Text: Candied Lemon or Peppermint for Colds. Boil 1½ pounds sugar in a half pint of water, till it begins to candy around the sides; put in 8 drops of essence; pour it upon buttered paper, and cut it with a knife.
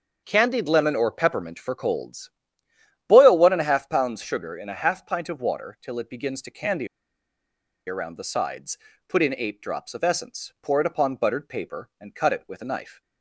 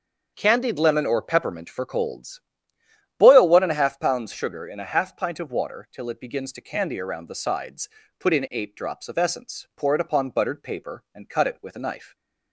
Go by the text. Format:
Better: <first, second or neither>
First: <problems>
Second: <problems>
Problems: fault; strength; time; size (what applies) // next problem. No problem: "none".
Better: second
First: starts louder than the rest; until 1.2 s; 7 dB // pauses between "candy" and "around"; at 6.8 s; 1.0 s long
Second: starts louder than the rest; until 1.3 s; 7 dB